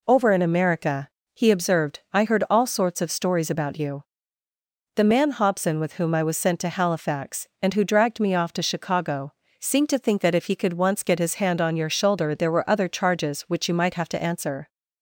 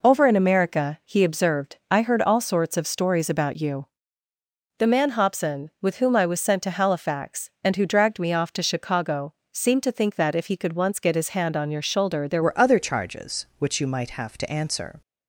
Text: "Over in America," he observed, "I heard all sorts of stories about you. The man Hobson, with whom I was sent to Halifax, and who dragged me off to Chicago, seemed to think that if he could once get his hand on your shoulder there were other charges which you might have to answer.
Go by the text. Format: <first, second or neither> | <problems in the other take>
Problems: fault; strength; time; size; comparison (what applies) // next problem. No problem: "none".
first | changes voice at "were"; from 12.4 s on; 2.6 s long